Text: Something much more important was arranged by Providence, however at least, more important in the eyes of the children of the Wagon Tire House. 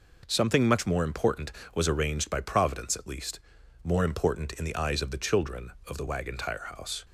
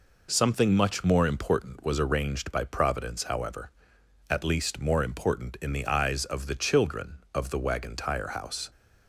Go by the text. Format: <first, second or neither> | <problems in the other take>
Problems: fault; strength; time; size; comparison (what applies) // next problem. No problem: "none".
second | skips "however"; at 2.9 s